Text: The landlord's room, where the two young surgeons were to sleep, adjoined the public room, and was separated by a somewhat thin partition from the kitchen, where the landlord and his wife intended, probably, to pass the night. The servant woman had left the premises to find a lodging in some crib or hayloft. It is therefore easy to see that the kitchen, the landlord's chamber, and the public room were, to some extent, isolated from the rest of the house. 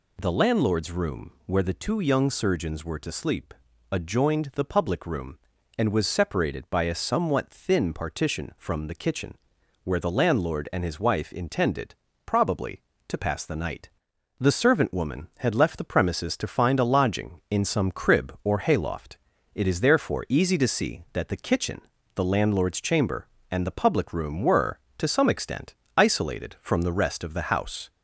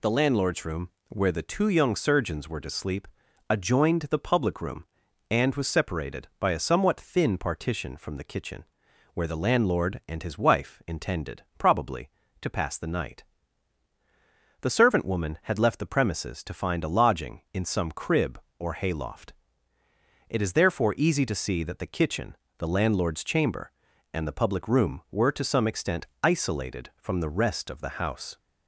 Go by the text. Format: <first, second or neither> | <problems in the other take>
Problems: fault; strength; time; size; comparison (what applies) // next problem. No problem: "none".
neither | none